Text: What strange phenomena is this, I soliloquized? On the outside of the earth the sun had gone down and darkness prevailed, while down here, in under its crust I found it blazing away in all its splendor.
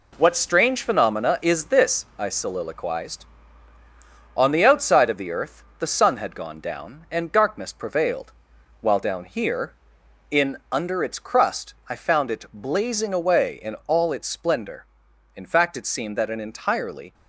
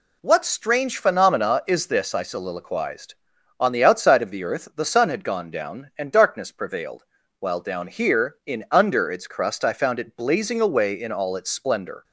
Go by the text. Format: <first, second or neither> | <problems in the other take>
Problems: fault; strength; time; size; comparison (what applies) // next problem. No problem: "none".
second | pauses between "earth" and "the"; slight; at 5.6 s; 0.16 s long // pauses between "crust" and "I"; slight; at 11.7 s; 0.16 s long // goes on to say "In fact it seemed that an entirely"; strong; from 15.3 s on; 1.7 s long